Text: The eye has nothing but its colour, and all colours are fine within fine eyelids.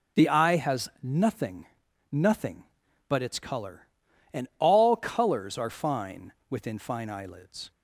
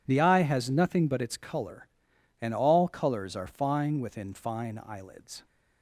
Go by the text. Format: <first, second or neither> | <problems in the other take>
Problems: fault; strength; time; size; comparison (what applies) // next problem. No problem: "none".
second | says "nothing" twice; at 2.1 s // pauses between "fine" and "within"; slight; at 6.3 s; 0.16 s long